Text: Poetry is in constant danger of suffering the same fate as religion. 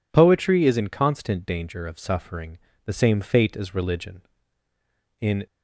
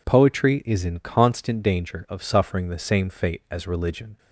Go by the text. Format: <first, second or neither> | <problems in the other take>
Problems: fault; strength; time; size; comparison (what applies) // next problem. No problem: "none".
second | pauses between "suffering" and "the"; slight; at 2.5 s; 0.26 s long // goes on to say "In"; slight; from 5.1 s on; 0.26 s long